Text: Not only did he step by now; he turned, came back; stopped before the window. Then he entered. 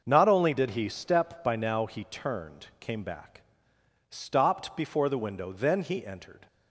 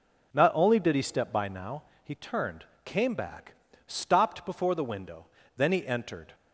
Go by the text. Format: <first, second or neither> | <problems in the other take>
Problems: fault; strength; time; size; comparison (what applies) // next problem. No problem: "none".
neither | none